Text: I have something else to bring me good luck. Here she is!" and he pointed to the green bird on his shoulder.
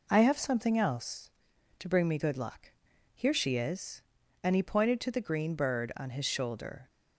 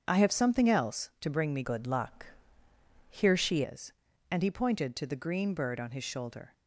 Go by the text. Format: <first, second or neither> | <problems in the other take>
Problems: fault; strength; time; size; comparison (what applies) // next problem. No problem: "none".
first | starts louder than the rest; strong; until 1.0 s; 7.5 dB // changes voice from "good" to "she"; from 1.6 to 3.6 s; 2.0 s long